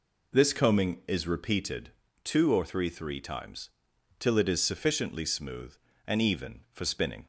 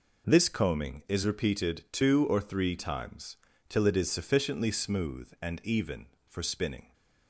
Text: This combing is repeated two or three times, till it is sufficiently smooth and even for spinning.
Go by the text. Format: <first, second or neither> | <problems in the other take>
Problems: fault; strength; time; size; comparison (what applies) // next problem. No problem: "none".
second | pauses between "repeated" and "two"; slight; at 1.8 s; 0.34 s long // says "three" twice; at 2.8 s